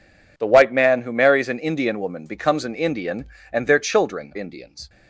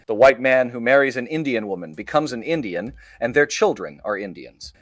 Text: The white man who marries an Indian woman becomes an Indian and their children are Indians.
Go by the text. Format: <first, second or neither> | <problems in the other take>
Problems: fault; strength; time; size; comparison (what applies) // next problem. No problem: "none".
second | skips "are"; at 4.3 s